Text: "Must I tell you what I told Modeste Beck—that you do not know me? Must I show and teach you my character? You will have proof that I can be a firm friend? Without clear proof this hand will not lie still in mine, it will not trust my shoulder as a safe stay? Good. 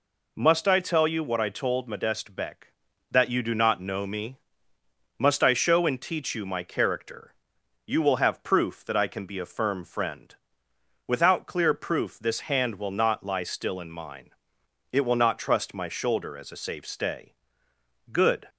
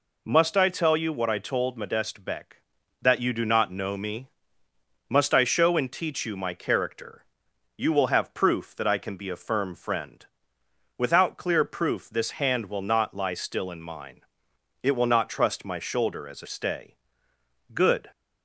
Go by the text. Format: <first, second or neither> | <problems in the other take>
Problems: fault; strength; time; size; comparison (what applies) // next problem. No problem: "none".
first | skips "safe"; at 16.4 s